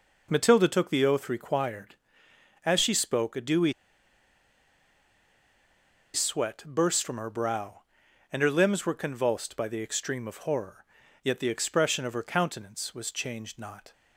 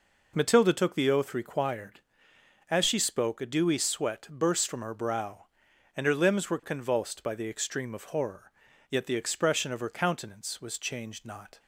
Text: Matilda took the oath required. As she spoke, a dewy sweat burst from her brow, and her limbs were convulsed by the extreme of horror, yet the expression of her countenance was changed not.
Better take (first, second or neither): second